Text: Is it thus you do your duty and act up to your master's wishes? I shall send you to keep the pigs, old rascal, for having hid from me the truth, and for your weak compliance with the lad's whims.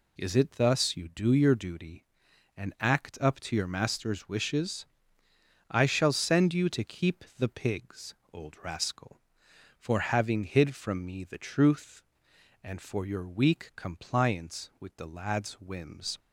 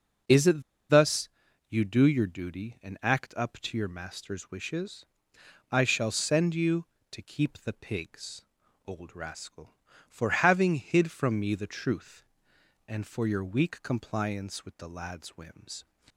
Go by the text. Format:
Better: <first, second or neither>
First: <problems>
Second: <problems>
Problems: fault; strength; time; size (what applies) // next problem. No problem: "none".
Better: first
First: none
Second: pauses between "it" and "thus"; slight; at 0.6 s; 0.27 s long // pauses between "thus" and "you"; at 1.2 s; 0.42 s long